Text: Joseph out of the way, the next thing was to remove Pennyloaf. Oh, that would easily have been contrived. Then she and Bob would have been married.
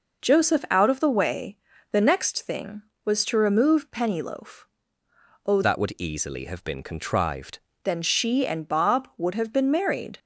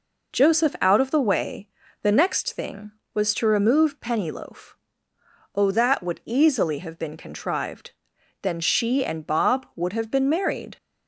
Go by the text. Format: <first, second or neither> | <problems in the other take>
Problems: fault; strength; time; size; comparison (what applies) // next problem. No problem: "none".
second | changes voice from "that" to "contrived"; from 5.6 to 7.5 s; 1.9 s long